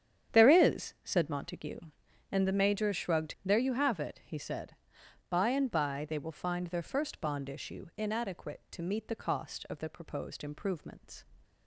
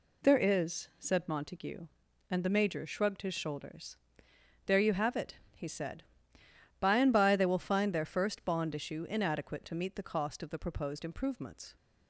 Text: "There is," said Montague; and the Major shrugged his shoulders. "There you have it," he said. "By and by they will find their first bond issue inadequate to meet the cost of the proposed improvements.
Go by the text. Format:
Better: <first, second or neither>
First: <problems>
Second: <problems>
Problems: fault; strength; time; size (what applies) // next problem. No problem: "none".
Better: second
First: starts louder than the rest; strong; until 1.4 s; 9 dB // skips "his shoulders"; at 3.3 s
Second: none